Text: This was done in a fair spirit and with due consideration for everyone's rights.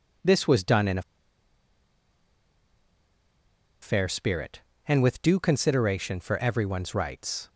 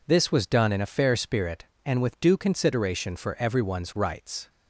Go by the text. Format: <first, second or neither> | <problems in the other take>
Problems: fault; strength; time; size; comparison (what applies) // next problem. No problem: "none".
second | pauses between "a" and "fair"; strong; at 1.0 s; 2.8 s long